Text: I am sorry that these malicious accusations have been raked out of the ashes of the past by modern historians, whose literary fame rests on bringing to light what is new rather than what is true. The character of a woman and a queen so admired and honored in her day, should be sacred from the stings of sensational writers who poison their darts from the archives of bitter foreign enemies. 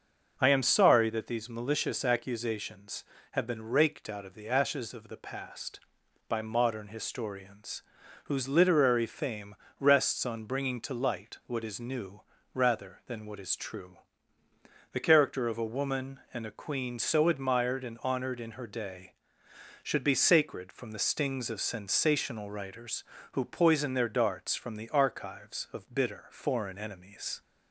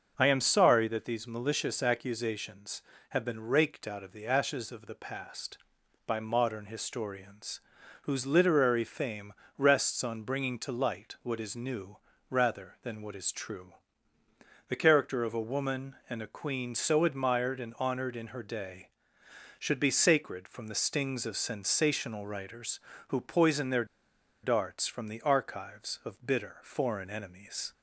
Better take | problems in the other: first | starts louder than the rest; until 1.1 s; 6.5 dB; also in the first // pauses between "fame" and "rests"; slight; at 9.3 s; 0.24 s long; slight in the first // pauses between "new" and "rather"; slight; at 11.9 s; 0.32 s long; slight in the first // pauses between "their" and "darts"; noticeable; at 23.8 s; 0.58 s long

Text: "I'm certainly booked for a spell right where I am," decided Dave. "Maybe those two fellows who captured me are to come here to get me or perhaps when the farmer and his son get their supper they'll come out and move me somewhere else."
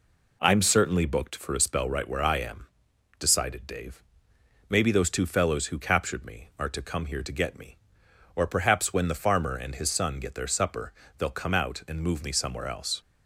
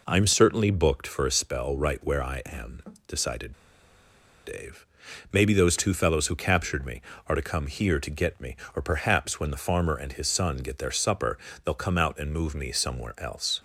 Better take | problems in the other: first | pauses between "decided" and "Dave"; noticeable; at 3.5 s; 0.91 s long // pauses between "supper" and "they'll"; slight; at 11.3 s; 0.28 s long; slight in the first

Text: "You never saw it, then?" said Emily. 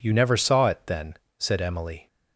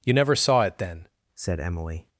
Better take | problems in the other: first | changes voice at "said"; from 1.3 s on; 0.7 s long

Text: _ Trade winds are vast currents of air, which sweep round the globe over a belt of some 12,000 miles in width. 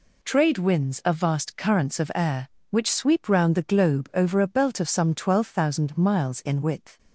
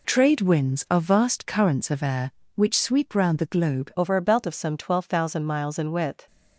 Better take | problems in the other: first | changes voice at "over"; from 3.9 s on; 2.3 s long

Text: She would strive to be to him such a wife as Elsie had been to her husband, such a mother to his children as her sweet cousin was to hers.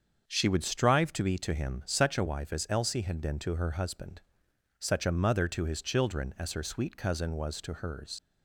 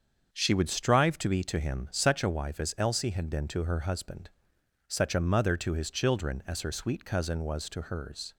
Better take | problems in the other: second | starts louder than the rest; until 1.2 s; 7 dB; also in the second // leaves "hers" unfinished; at 8.1 s; 65 ms

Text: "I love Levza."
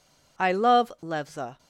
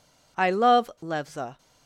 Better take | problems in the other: neither | none

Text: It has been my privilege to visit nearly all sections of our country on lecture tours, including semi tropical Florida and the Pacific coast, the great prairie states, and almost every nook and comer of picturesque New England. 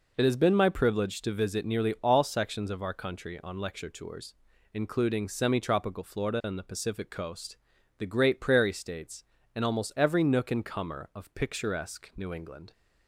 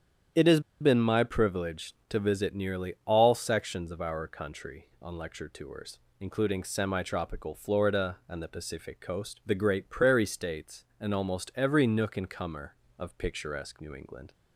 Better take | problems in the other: first | starts louder than the rest; strong; until 1.5 s; 8.5 dB // pauses between "has" and "been"; slight; at 0.5 s; 0.20 s long

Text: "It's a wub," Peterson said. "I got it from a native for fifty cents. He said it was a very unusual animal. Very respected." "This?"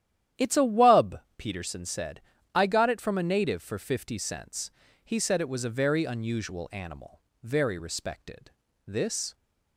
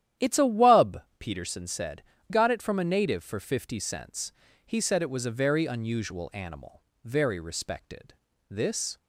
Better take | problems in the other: first | starts louder than the rest; strong; until 1.3 s; 11 dB; strong in the first // skips "I"; at 2.1 s

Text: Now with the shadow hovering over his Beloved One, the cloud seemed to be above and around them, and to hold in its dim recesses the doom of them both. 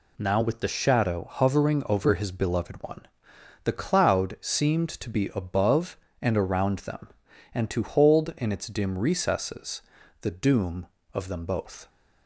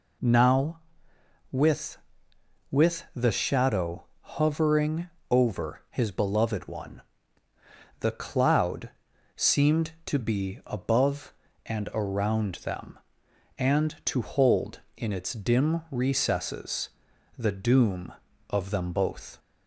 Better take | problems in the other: first | says "with" twice; at 2.7 s // pauses between "shadow" and "hovering"; slight; at 4.0 s; 0.18 s long // pauses between "hovering" and "over"; slight; at 5.0 s; 0.22 s long // pauses between "cloud" and "seemed"; noticeable; at 8.8 s; 0.48 s long // pauses between "recesses" and "the"; noticeable; at 16.8 s; 0.48 s long; also in the first

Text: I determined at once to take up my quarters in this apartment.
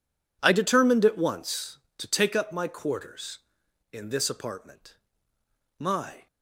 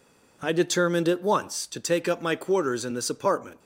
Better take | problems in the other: second | goes on to say "My"; slight; from 5.7 s on; 0.48 s long

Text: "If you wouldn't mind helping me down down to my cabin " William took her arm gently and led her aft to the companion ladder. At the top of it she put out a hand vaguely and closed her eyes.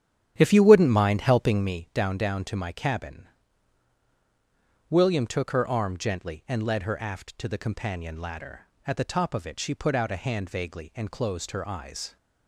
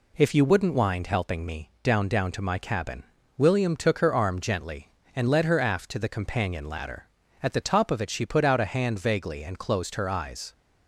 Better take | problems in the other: second | starts louder than the rest; strong; until 1.7 s; 10 dB

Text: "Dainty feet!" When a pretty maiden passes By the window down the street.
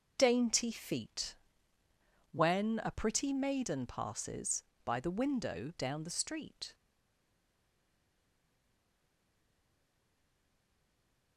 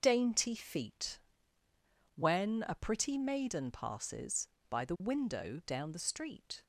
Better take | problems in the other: second | starts louder than the rest; noticeable; until 1.2 s; 6 dB; noticeable in the second // stays silent after the last word; strong; from 6.7 s on; 4.6 s long

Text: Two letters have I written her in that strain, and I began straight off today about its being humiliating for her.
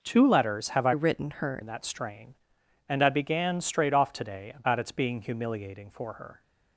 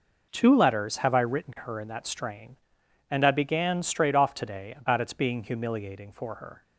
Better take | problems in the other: second | changes voice from "written" to "her"; from 0.9 to 1.6 s; 0.7 s long

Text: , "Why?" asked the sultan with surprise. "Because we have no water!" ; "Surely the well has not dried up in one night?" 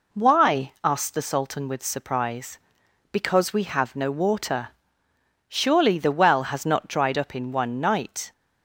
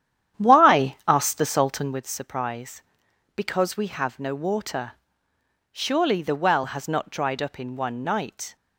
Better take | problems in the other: first | starts louder than the rest; strong; until 2.1 s; 10 dB

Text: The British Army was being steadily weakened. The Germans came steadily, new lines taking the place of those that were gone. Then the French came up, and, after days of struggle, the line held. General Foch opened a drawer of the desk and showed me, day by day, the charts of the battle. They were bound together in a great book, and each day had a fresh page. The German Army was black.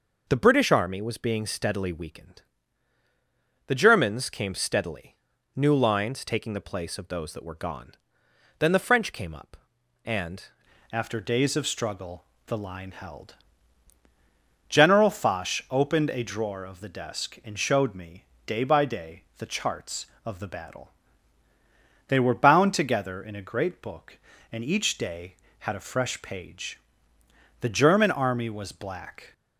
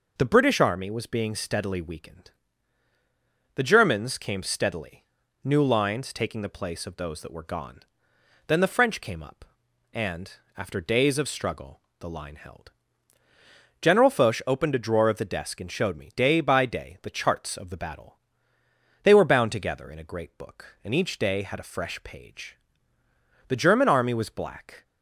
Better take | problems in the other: second | changes voice at "after"; from 10.9 s on; 18.4 s long

